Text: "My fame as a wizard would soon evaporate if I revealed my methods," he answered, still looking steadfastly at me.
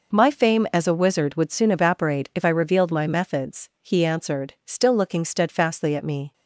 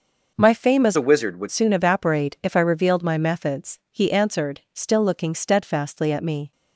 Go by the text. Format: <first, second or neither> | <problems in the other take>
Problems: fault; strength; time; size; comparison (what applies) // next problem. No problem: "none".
first | changes voice from "a" to "would"; from 0.9 to 1.4 s; 0.5 s long